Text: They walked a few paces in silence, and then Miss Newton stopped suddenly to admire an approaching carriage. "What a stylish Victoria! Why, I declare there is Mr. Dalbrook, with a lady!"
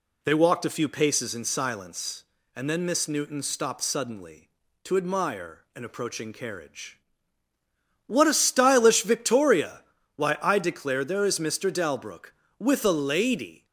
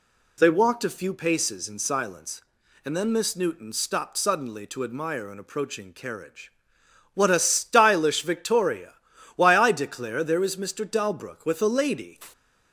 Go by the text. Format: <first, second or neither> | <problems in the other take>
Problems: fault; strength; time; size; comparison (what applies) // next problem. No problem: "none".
neither | none